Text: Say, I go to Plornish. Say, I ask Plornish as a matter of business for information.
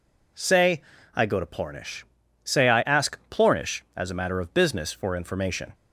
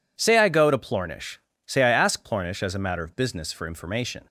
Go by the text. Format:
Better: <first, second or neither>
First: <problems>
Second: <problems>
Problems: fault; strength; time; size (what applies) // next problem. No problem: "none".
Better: neither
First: none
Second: none